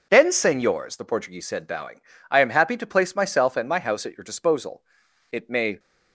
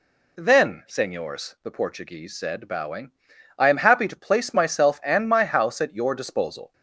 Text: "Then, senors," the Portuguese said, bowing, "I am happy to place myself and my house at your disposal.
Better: second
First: goes on to say "It may"; slight; from 5.3 s on; 0.48 s long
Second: none

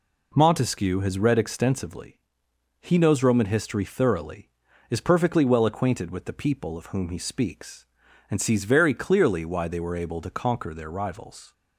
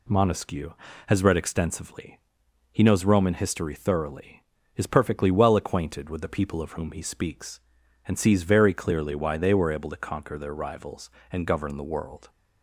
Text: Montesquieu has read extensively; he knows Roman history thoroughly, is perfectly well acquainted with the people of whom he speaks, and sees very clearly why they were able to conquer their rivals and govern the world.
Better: second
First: stops before "and govern the world"; at 11.5 s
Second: none

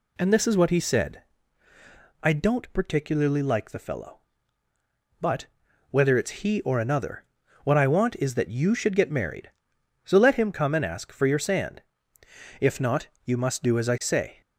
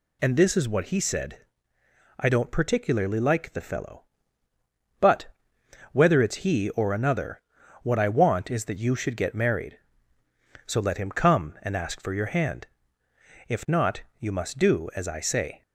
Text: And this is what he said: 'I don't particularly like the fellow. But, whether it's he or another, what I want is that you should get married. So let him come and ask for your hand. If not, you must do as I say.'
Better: second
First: says "sand" for "hand"; at 11.3 s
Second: none

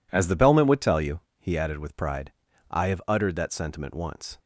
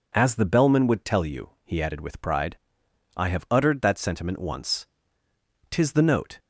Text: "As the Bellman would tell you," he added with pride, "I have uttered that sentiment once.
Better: first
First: none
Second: goes on to say "Tis the note"; noticeable; from 5.7 s on; 0.66 s long

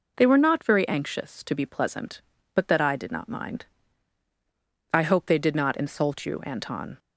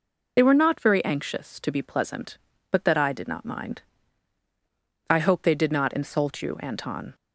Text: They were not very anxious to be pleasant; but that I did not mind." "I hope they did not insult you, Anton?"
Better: first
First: none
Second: loses the start of "They"; at 0.3 s; 45 ms

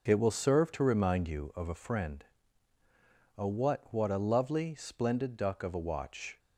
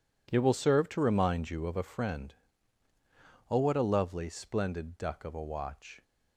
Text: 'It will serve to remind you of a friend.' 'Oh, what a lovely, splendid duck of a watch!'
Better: second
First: says "what" twice; at 3.9 s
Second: none

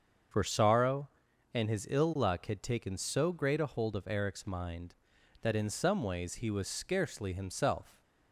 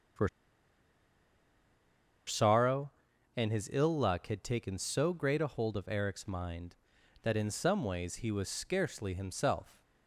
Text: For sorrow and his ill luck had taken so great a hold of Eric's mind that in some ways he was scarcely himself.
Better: first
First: starts louder than the rest; until 1.7 s; 7 dB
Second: starts louder than the rest; until 3.5 s; 7 dB // pauses between "For" and "sorrow"; strong; at 0.2 s; 1.9 s long

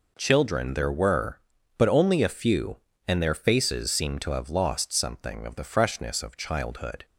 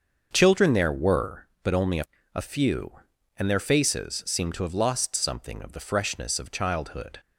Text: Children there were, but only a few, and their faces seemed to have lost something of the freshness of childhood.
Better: first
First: none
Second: starts louder than the rest; until 1.3 s; 6.5 dB // says "a" twice; at 2.3 s

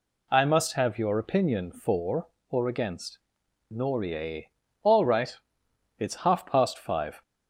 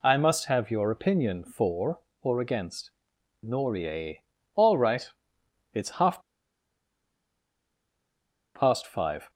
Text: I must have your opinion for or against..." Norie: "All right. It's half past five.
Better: first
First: none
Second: pauses between "half" and "past"; strong; at 6.2 s; 2.3 s long

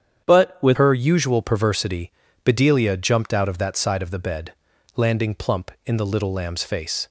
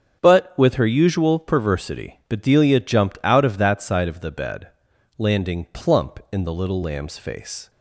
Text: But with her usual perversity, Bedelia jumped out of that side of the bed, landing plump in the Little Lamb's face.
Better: second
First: starts louder than the rest; strong; until 1.2 s; 8.5 dB // changes voice at "her"; from 0.7 s on; 6.3 s long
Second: starts louder than the rest; until 1.2 s; 6.5 dB

